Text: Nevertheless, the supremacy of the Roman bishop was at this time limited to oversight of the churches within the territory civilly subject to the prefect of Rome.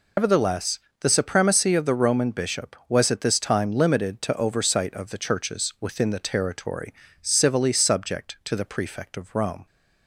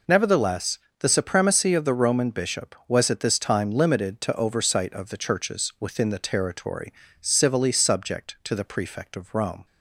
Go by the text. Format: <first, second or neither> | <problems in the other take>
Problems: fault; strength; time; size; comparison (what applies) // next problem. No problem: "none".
second | loses the start of "Nevertheless"; at 0.1 s; 95 ms // pauses between "territory" and "civilly"; slight; at 6.9 s; 0.28 s long; slight in the second